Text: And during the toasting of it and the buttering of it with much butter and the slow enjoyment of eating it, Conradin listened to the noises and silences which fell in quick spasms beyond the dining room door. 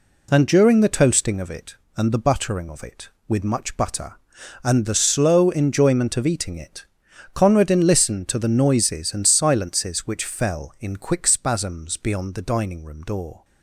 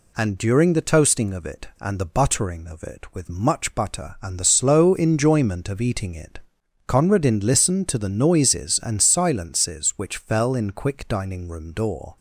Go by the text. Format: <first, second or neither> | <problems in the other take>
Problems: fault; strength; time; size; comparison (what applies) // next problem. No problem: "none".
first | skips "spasms beyond the"; at 11.0 s